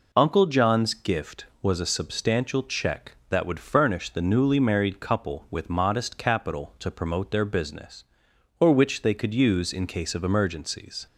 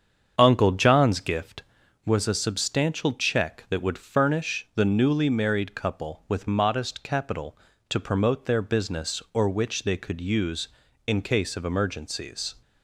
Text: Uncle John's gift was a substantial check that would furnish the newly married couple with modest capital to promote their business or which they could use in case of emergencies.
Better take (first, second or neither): first